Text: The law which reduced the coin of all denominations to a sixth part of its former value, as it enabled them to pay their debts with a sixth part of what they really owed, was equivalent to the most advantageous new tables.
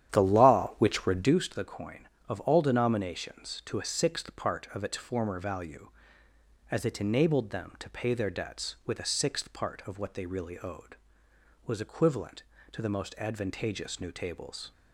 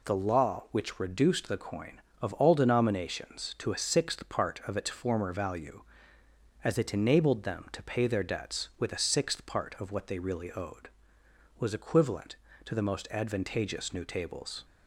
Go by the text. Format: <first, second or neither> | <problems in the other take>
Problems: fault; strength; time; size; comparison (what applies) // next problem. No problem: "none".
second | starts louder than the rest; strong; until 1.4 s; 10.5 dB